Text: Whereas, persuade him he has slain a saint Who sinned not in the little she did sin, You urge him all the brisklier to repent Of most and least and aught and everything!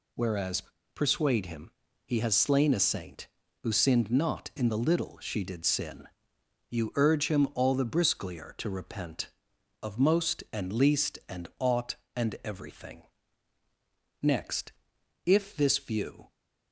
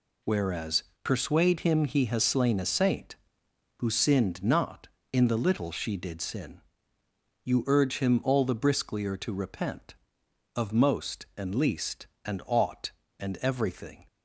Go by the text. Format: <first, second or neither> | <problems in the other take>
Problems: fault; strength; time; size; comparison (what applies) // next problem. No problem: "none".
second | pauses between "him" and "he"; slight; at 1.7 s; 0.32 s long // goes on to say "Next if this view"; strong; from 14.2 s on; 2.0 s long